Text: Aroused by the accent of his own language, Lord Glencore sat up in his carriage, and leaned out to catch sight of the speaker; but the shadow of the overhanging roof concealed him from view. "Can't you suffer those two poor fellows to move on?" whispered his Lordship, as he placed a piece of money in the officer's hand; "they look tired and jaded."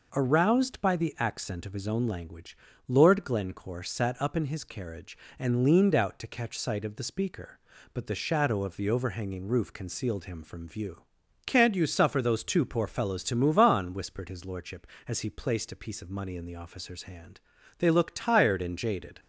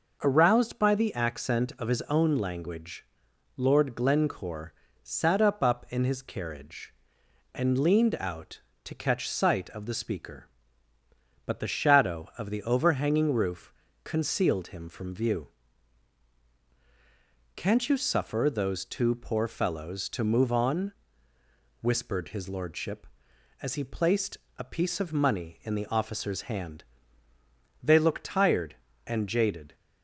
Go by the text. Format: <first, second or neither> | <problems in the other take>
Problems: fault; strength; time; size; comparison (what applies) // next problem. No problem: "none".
first | pauses between "Glencore" and "sat"; slight; at 4.7 s; 0.30 s long // says "up" twice; at 5.6 s // pauses between "roof" and "concealed"; slight; at 13.7 s; 0.30 s long // pauses between "placed" and "a"; slight; at 24.3 s; 0.18 s long